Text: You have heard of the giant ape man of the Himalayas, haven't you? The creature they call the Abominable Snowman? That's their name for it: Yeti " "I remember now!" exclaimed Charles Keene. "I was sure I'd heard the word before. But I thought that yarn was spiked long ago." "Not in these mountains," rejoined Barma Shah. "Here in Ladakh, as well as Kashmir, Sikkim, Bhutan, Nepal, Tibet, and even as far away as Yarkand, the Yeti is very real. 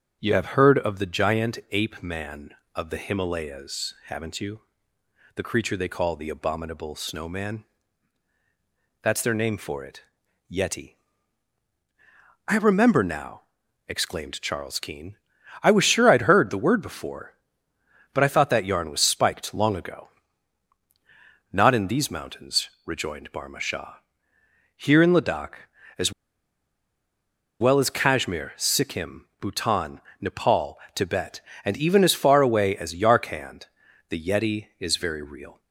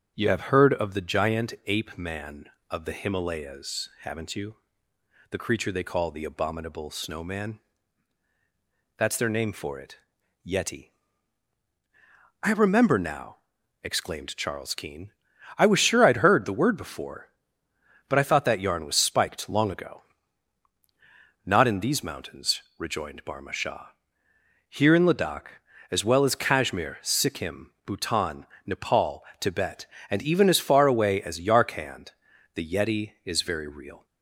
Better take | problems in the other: second | starts louder than the rest; strong; until 1.2 s; 8 dB; strong in the second // pauses between "as" and "well"; strong; at 26.1 s; 1.4 s long

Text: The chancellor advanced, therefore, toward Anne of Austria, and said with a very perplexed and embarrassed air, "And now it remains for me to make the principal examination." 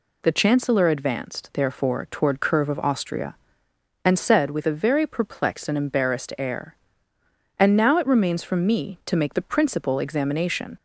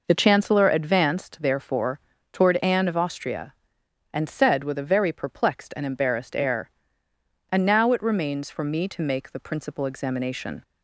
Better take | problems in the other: second | says "Curve" for "Anne"; at 2.4 s

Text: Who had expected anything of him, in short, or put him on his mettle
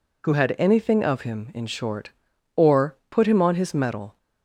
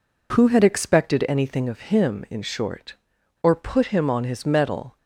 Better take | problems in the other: second | skips "expected"; at 0.5 s

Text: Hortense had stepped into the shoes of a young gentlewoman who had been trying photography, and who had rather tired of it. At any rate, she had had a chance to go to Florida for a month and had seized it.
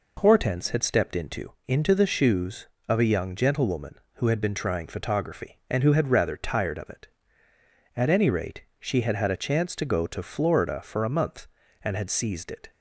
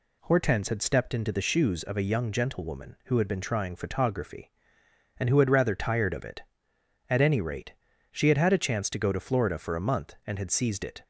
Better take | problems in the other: second | says "into" twice; at 1.6 s

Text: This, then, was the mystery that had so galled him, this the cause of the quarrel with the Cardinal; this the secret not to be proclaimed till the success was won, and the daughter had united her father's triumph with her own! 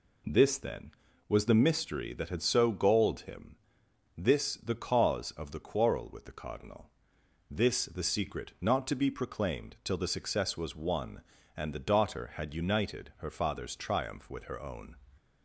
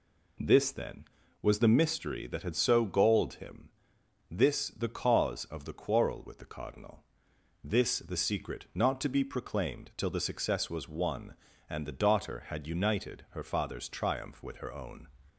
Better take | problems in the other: neither | none

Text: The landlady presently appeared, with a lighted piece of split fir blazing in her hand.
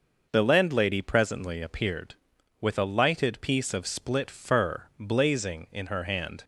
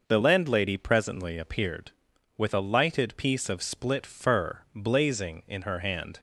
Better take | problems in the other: neither | none

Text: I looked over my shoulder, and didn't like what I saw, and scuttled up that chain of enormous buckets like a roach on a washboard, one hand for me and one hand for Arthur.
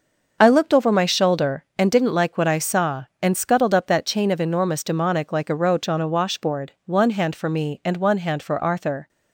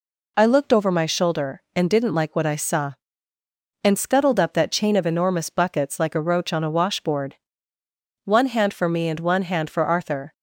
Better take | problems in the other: second | starts louder than the rest; noticeable; until 1.4 s; 6 dB // says "demonic" for "buckets"; at 4.8 s

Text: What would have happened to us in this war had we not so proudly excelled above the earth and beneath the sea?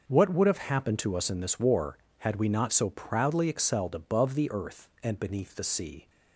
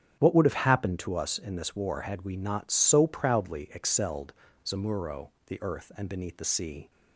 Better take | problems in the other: first | starts louder than the rest; strong; until 1.2 s; 8.5 dB; noticeable in the first // says "zamuro" for "above"; at 4.6 s

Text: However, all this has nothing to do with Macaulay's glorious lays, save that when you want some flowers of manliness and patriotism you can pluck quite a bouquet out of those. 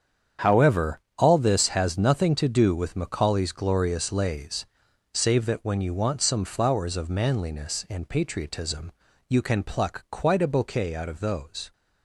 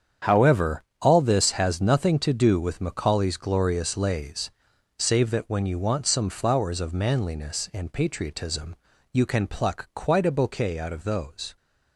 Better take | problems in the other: neither | starts louder than the rest; strong; the same in both // pauses between "patriotism" and "you"; slight; the same in both

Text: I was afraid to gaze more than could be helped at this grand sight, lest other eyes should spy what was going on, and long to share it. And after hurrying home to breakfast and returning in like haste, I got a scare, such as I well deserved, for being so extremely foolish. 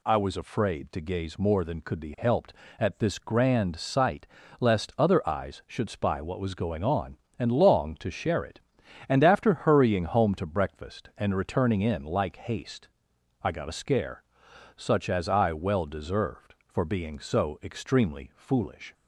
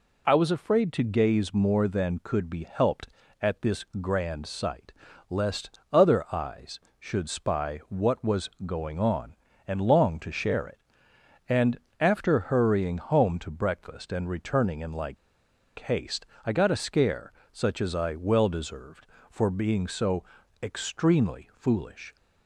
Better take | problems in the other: first | pauses between "this" and "grand"; slight; at 3.8 s; 0.16 s long // pauses between "And" and "after"; slight; at 11.7 s; 0.22 s long // pauses between "like" and "haste"; noticeable; at 15.1 s; 0.62 s long // pauses between "so" and "extremely"; at 20.2 s; 0.40 s long

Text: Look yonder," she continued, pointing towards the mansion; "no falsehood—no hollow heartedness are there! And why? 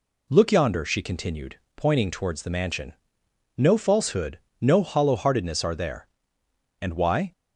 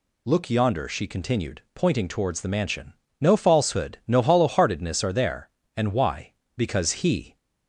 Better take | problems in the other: first | goes on to say "Because he"; noticeable; from 6.5 s on; 0.80 s long

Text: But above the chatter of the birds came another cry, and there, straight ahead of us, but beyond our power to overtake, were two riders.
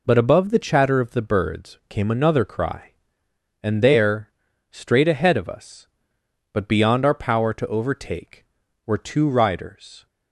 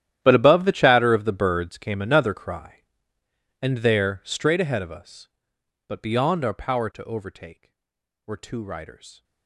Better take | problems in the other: first | gets quieter; strong; throughout; 19.5 dB

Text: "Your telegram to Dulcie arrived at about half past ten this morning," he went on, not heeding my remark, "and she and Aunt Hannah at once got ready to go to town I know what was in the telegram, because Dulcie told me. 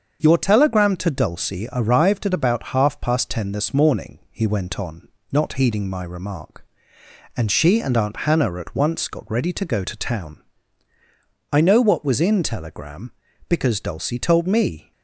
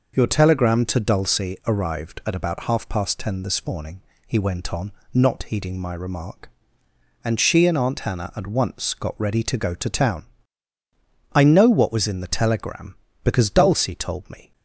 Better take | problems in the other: second | starts louder than the rest; until 1.2 s; 7 dB // pauses between "town" and "I"; at 10.4 s; 1.1 s long; also in the second // skips "the"; at 12.4 s

